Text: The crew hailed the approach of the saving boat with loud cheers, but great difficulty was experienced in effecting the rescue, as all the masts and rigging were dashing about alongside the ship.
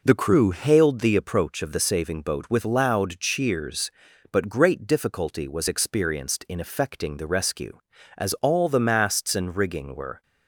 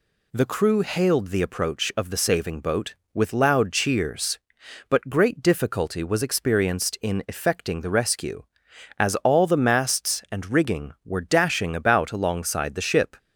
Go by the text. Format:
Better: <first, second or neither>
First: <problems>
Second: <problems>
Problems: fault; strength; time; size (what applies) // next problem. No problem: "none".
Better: second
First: stops before "dashing about alongside the ship"; at 10.2 s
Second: none